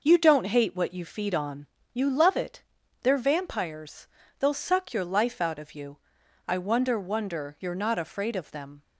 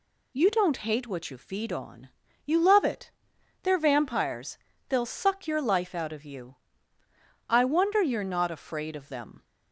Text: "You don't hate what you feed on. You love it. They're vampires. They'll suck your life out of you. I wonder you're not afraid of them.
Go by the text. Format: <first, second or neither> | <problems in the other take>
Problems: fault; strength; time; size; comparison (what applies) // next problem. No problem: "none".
second | says "wonder" twice; at 6.9 s